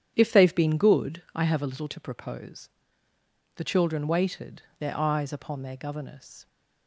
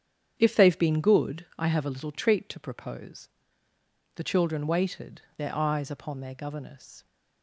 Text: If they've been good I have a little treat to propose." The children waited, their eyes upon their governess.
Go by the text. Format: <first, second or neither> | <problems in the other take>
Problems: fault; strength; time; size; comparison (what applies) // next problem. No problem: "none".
second | starts louder than the rest; strong; until 1.1 s; 9.5 dB; strong in the second // skips "treat"; at 1.8 s